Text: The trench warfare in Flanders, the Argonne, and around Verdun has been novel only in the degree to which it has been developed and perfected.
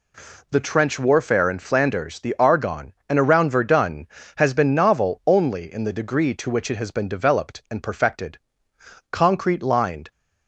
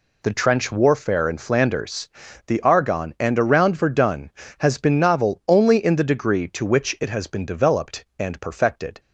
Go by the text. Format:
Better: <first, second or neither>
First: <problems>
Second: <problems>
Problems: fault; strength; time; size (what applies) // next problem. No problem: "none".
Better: second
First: goes on to say "Concrete lined"; noticeable; from 9.1 s on; 1.0 s long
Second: none